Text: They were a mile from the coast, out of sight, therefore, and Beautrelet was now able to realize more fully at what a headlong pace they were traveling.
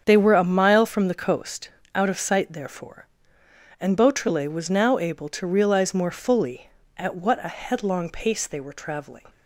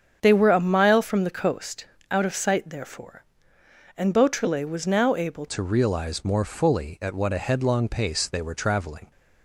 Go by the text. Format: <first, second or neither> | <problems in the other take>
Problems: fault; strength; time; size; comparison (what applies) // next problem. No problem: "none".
first | starts louder than the rest; strong; until 1.2 s; 7.5 dB; strong in the first // changes voice at "to"; from 5.4 s on; 3.7 s long